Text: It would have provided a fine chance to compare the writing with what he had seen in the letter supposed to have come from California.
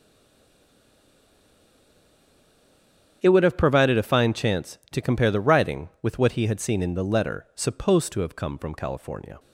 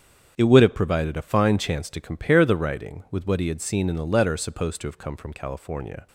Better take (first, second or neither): second